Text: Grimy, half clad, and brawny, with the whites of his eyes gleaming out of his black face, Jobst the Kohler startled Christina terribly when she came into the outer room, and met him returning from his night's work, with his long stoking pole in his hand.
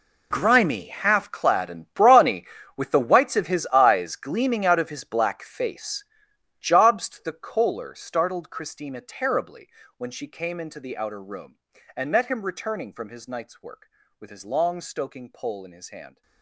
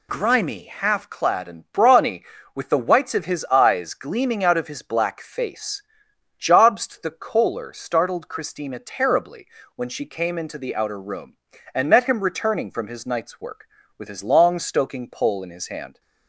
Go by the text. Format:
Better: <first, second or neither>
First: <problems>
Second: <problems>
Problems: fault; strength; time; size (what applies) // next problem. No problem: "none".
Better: second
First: gets quieter; strong; throughout; 15.5 dB // pauses between "terribly" and "when"; slight; at 9.6 s; 0.30 s long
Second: pauses between "terribly" and "when"; slight; at 9.4 s; 0.30 s long